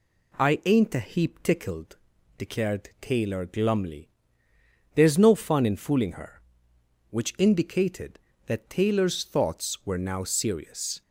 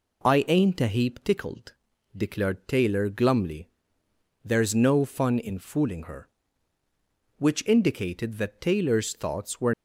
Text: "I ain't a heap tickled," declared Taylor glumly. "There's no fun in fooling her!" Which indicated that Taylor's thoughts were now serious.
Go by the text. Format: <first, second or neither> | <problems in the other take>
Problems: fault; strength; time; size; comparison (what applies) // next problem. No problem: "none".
first | stops before "now serious"; at 9.7 s